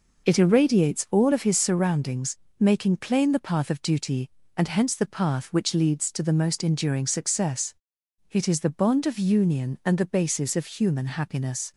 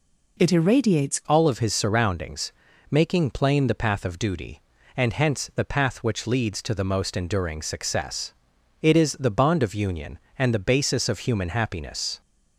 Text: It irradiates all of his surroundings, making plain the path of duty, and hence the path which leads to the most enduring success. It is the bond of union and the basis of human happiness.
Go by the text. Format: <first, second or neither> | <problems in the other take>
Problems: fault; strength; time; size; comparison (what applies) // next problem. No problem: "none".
first | changes voice at "all"; from 1.2 s on; 11.0 s long